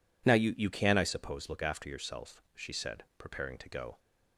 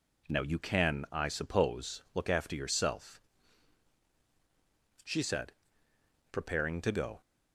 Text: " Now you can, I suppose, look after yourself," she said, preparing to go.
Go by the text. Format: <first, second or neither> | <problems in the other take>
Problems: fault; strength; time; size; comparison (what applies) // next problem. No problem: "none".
second | says "you" twice; at 0.5 s